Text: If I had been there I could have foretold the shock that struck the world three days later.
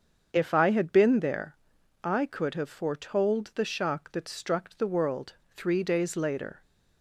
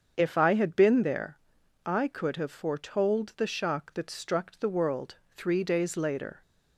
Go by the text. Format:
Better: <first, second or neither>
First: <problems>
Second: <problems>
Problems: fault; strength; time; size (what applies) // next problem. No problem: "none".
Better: neither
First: starts louder than the rest; until 1.3 s; 7 dB // pauses between "there" and "I"; noticeable; at 1.5 s; 0.48 s long // pauses between "world" and "three"; slight; at 5.3 s; 0.19 s long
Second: starts louder than the rest; strong; until 1.2 s; 7 dB // pauses between "there" and "I"; noticeable; at 1.3 s; 0.48 s long // pauses between "world" and "three"; slight; at 5.1 s; 0.18 s long